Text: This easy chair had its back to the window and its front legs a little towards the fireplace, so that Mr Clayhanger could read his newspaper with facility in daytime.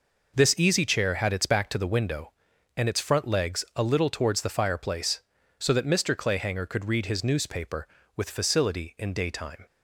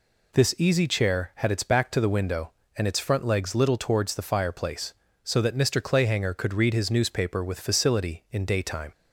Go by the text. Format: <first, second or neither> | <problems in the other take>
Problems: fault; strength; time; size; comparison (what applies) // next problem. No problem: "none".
first | skips "a"; at 3.5 s